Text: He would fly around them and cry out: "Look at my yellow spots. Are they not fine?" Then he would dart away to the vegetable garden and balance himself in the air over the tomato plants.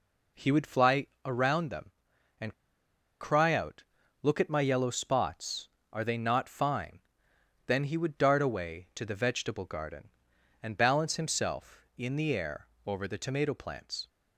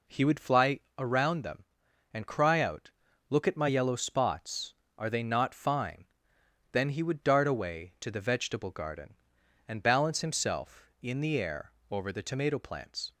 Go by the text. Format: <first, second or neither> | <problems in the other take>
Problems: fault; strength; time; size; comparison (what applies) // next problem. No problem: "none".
second | pauses between "fly" and "around"; slight; at 1.0 s; 0.18 s long; slight in the second // pauses between "and" and "cry"; noticeable; at 2.5 s; 0.68 s long // pauses between "air" and "over"; slight; at 12.6 s; 0.18 s long; slight in the second